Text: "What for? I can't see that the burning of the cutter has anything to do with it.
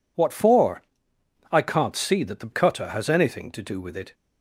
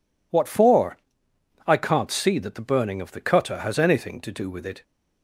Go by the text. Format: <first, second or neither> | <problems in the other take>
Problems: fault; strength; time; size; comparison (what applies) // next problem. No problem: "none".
second | skips "burning of the"; at 2.5 s